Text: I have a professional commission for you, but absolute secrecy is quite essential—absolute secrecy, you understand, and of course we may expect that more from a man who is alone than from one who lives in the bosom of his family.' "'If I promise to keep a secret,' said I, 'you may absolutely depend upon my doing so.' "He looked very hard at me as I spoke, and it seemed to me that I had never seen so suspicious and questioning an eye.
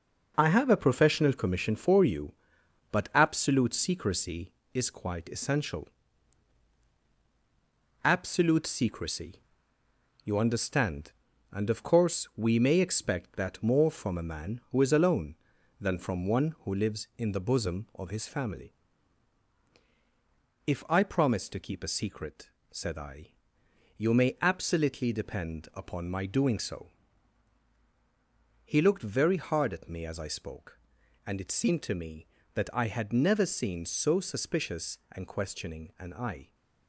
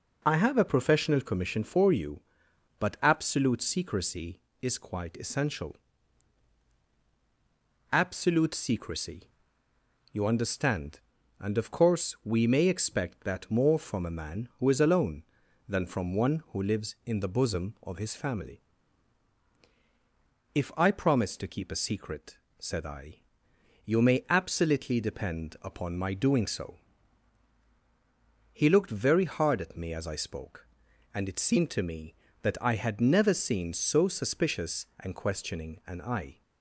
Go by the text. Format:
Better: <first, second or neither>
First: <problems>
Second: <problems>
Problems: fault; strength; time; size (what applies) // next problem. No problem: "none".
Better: second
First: gets quieter; throughout; 6.5 dB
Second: none